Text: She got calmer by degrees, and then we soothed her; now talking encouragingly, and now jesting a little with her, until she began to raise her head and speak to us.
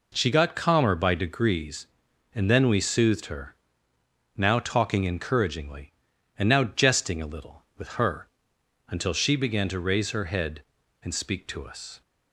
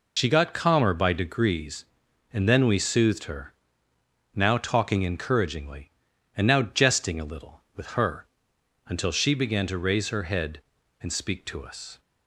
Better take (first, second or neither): first